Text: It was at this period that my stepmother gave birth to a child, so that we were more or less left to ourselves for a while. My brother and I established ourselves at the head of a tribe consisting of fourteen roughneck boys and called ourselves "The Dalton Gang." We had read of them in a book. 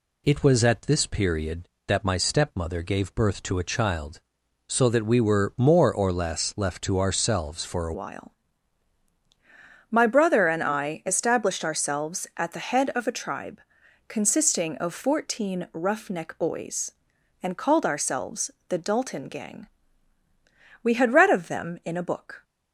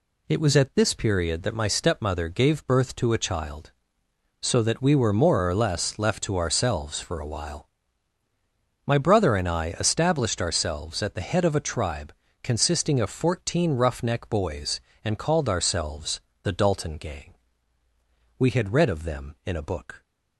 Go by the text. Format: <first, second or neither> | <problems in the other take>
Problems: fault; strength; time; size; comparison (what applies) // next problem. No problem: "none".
second | changes voice at "while"; from 7.9 s on; 14.5 s long // pauses between "tribe" and "consisting"; noticeable; at 13.6 s; 0.46 s long; slight in the second // pauses between "ourselves" and "The"; slight; at 18.4 s; 0.20 s long; slight in the second